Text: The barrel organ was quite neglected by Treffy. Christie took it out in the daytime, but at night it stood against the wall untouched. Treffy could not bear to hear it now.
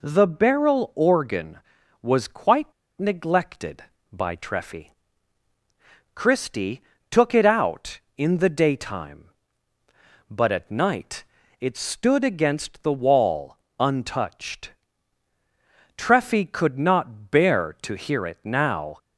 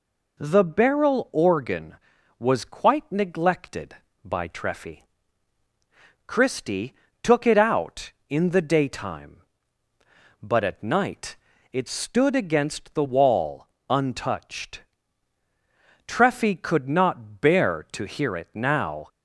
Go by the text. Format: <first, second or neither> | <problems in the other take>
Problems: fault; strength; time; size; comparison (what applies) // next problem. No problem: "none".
second | pauses between "quite" and "neglected"; slight; at 2.7 s; 0.25 s long // pauses between "Christie" and "took"; slight; at 6.8 s; 0.30 s long; slight in the second // pauses between "night" and "it"; at 11.2 s; 0.38 s long; also in the second // pauses between "wall" and "untouched"; slight; at 13.5 s; 0.22 s long; slight in the second